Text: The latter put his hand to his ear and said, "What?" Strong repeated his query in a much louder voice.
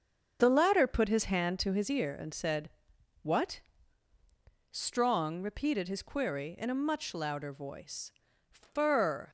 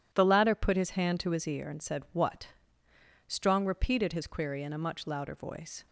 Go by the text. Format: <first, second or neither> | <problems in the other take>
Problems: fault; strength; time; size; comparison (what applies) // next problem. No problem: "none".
second | starts louder than the rest; until 1.4 s; 6.5 dB // goes on to say "Fur"; noticeable; from 8.4 s on; 0.80 s long